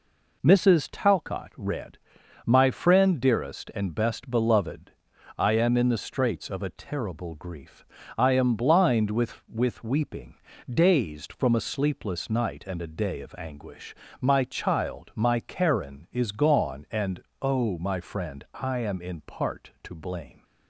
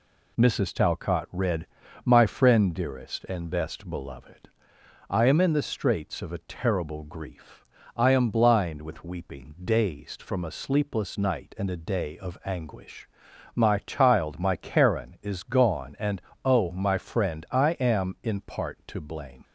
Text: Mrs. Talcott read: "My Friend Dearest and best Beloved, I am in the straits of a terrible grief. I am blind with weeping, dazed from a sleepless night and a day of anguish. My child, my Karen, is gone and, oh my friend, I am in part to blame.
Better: second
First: says "with" twice; at 9.4 s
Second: none

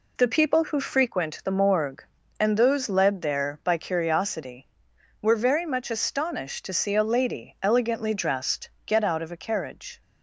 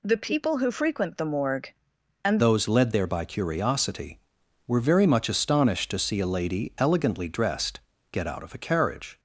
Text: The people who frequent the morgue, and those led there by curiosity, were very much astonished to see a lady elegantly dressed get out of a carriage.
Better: first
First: pauses between "dressed" and "get"; slight; at 8.6 s; 0.15 s long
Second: changes voice at "those"; from 2.3 s on; 6.8 s long // pauses between "dressed" and "get"; slight; at 7.7 s; 0.30 s long

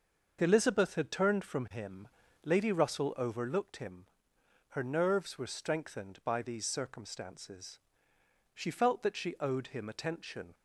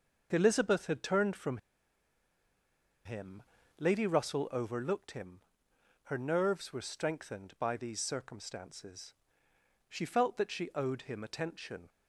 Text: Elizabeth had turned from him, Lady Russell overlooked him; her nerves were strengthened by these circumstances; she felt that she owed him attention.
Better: first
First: starts louder than the rest; noticeable; until 1.4 s; 6 dB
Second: starts louder than the rest; noticeable; until 1.3 s; 6 dB // pauses between "from" and "him"; strong; at 1.5 s; 1.4 s long

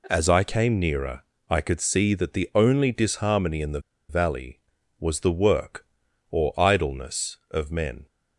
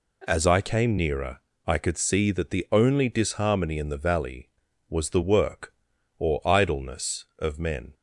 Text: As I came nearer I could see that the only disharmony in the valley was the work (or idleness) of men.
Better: second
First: pauses between "nearer" and "I"; slight; at 1.2 s; 0.26 s long // pauses between "the" and "valley"; slight; at 3.7 s; 0.30 s long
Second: pauses between "nearer" and "I"; slight; at 1.3 s; 0.26 s long

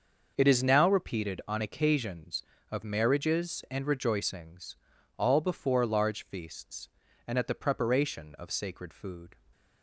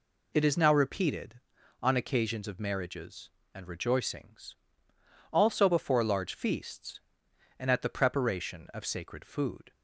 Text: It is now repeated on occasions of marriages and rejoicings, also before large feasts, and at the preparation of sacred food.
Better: second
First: starts louder than the rest; until 1.3 s; 6 dB // says "all" for "also"; at 5.1 s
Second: none

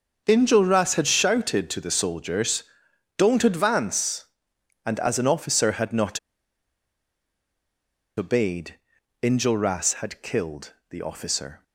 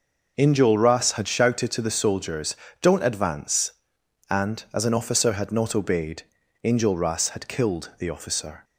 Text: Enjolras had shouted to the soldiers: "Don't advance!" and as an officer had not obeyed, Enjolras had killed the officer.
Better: second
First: starts louder than the rest; until 1.2 s; 6.5 dB // pauses between "not" and "obeyed"; strong; at 6.1 s; 1.9 s long // pauses between "killed" and "the"; slight; at 10.7 s; 0.18 s long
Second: none

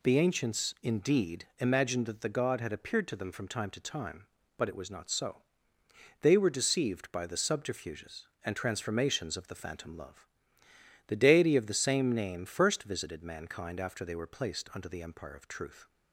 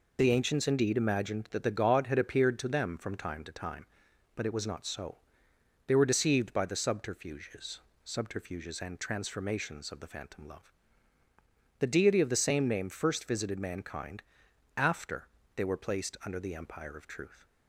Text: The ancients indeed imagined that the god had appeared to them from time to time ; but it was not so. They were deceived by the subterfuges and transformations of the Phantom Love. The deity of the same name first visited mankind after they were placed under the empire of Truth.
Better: first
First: none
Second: says "subterfuges" twice; at 8.0 s // pauses between "mankind" and "after"; noticeable; at 14.2 s; 0.52 s long // pauses between "after" and "they"; slight; at 15.2 s; 0.26 s long

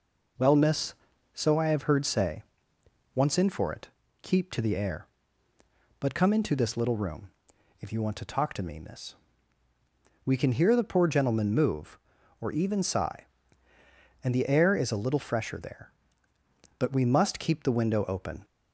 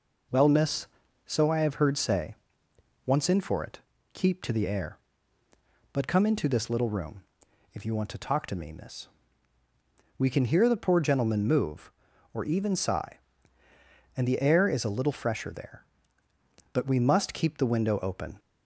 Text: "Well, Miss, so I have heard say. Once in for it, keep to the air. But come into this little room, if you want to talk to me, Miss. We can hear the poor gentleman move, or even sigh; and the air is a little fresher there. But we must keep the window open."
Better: neither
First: none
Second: none

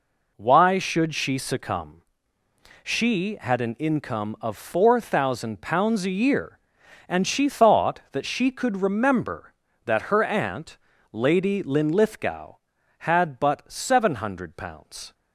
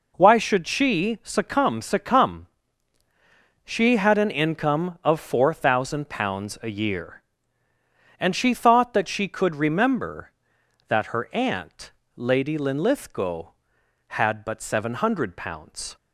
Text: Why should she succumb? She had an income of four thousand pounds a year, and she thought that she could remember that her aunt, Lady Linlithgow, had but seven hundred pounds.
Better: first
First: none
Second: says "succumb" twice; at 1.8 s

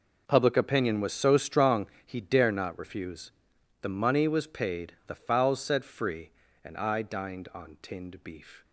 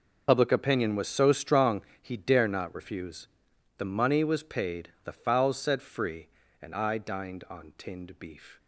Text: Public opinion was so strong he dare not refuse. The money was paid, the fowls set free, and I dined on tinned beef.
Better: first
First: pauses between "strong" and "he"; slight; at 1.8 s; 0.17 s long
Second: loses the start of "Public"; at 0.2 s; 60 ms // pauses between "strong" and "he"; slight; at 1.8 s; 0.18 s long

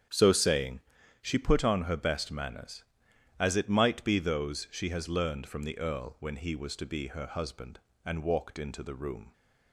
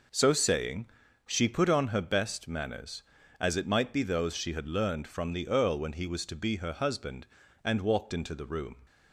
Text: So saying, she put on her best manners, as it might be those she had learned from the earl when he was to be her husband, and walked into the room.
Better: second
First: starts louder than the rest; strong; until 1.4 s; 8 dB // says "has" for "had"; at 4.9 s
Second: none

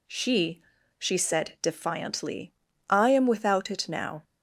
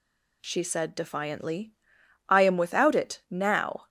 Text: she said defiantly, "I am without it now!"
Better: second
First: says "she" twice; at 0.9 s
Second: none

